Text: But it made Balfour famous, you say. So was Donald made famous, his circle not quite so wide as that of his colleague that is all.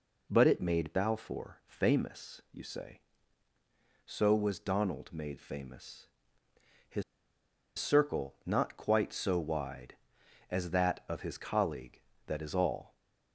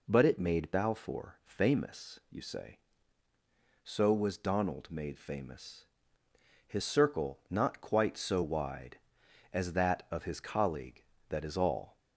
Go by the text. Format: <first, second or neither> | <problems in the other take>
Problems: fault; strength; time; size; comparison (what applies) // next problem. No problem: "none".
second | pauses between "his" and "circle"; noticeable; at 7.0 s; 0.75 s long